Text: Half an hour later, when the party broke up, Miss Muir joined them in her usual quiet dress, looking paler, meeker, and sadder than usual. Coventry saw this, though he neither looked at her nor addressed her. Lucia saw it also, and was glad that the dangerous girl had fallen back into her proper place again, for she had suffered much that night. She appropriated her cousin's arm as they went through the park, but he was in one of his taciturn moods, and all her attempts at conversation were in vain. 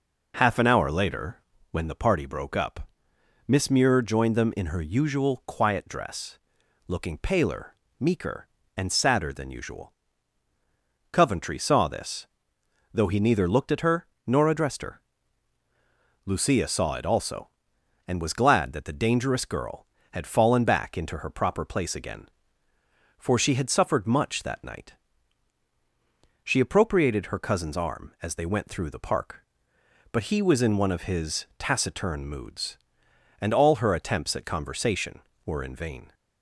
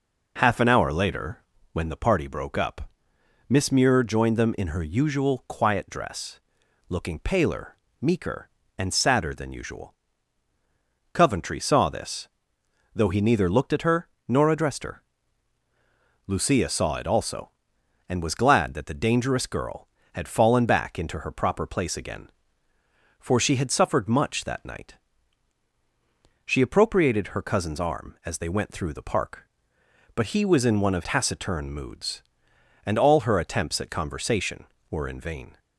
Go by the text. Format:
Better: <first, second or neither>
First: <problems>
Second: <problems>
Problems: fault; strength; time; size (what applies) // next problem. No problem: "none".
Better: first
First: pauses between "her" and "nor"; slight; at 14.0 s; 0.20 s long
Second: pauses between "her" and "nor"; slight; at 14.0 s; 0.20 s long // skips "his"; at 31.0 s